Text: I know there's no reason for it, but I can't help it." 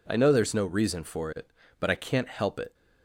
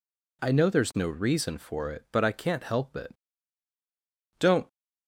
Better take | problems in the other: first | goes on to say "Don't"; slight; from 4.3 s on; 0.28 s long

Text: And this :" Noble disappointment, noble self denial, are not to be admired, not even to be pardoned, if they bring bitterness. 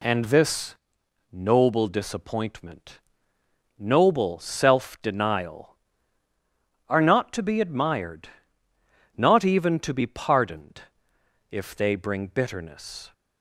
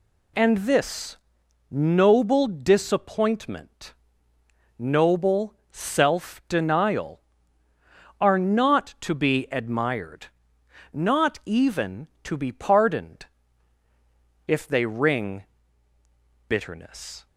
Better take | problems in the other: first | pauses between "noble" and "self"; slight; at 5.5 s; 0.16 s long // says "ring" for "bring"; at 14.8 s

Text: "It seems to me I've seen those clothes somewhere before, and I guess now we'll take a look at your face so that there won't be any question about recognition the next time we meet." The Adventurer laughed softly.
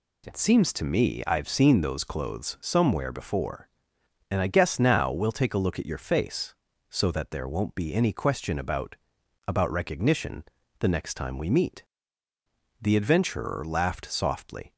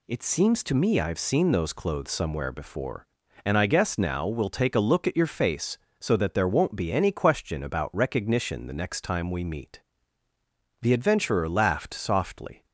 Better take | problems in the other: second | says "about" twice; at 9.4 s // pauses between "recognition" and "the"; slight; at 10.4 s; 0.36 s long

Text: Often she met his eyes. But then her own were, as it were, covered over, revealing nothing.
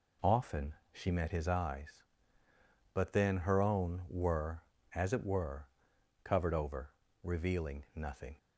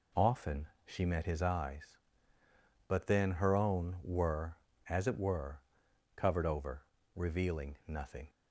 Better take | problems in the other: neither | pauses between "Often" and "she"; slight; the same in both

